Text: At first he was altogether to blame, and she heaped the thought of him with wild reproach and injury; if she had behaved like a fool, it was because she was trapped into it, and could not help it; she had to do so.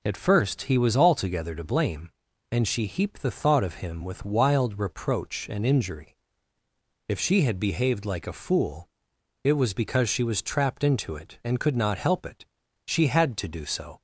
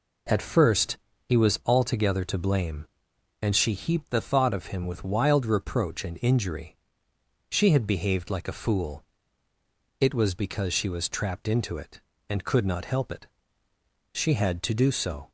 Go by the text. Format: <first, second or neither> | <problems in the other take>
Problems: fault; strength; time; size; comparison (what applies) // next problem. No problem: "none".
first | pauses between "first" and "he"; slight; at 0.9 s; 0.26 s long // skips "if"; at 7.1 s